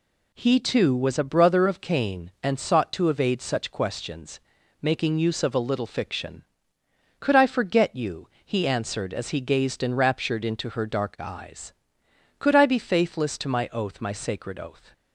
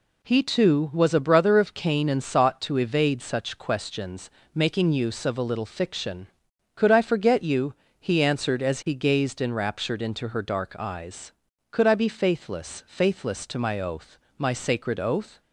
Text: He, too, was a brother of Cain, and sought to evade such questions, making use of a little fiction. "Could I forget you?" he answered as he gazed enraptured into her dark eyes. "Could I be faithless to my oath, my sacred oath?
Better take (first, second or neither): first